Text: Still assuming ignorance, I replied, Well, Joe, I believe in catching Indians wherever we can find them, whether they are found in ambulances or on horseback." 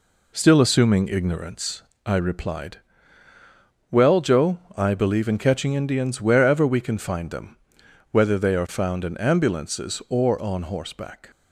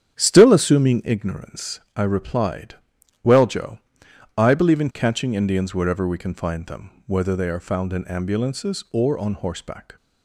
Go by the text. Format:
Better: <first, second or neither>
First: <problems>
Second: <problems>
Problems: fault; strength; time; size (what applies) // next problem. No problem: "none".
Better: first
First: none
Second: starts louder than the rest; strong; until 1.1 s; 9 dB